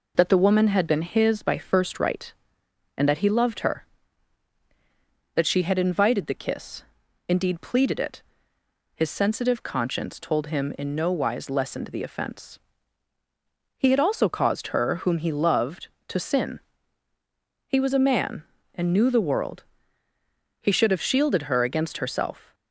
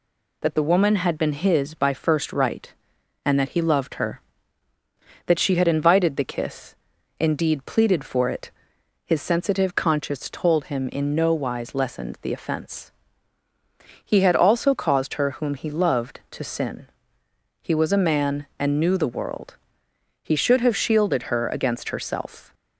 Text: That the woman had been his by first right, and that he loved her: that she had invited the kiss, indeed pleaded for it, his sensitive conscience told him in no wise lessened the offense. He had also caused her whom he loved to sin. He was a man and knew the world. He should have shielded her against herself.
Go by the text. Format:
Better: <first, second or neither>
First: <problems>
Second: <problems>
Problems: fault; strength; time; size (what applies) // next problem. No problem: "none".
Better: second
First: skips "for"; at 7.9 s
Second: none